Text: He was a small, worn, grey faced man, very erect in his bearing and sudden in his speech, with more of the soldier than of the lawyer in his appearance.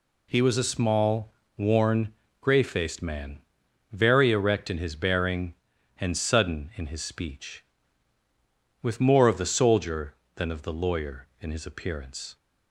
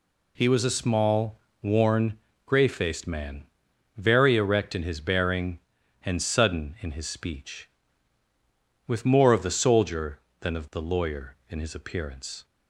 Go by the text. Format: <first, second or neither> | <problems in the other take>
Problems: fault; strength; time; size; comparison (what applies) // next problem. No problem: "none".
neither | none